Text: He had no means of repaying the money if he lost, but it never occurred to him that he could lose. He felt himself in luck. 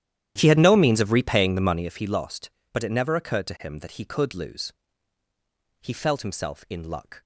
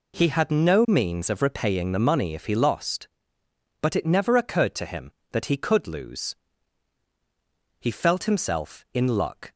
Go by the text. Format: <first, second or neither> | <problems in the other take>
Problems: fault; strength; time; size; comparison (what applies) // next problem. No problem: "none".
second | starts louder than the rest; strong; until 1.9 s; 11.5 dB